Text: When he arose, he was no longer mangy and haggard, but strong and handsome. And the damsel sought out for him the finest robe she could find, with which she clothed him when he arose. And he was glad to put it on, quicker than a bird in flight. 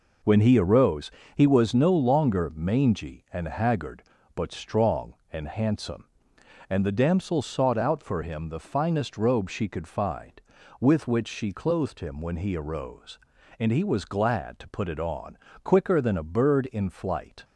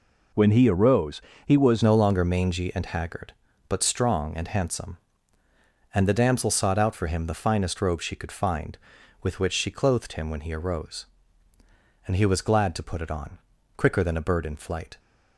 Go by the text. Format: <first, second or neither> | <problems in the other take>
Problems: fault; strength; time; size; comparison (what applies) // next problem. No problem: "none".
first | changes voice at "no"; from 1.8 s on; 13.1 s long